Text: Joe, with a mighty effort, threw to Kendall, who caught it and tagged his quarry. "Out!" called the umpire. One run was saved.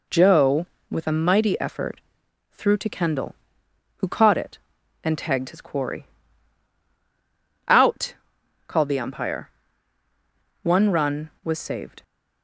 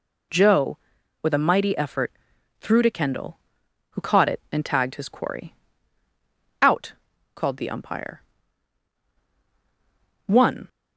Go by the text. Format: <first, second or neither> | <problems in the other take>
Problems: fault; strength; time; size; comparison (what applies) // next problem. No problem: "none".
first | stops before "run was saved"; at 10.6 s